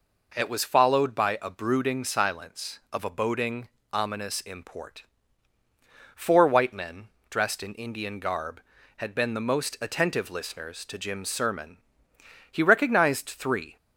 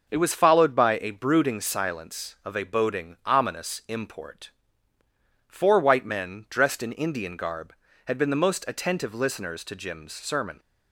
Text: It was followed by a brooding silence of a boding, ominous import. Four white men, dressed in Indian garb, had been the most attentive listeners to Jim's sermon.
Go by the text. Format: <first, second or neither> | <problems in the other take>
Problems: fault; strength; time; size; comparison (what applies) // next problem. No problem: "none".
second | goes on to say "He recognized three"; noticeable; from 12.5 s on; 1.2 s long